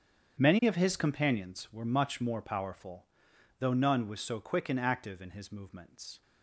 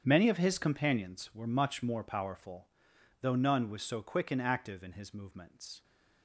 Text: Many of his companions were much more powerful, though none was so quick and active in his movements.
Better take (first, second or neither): neither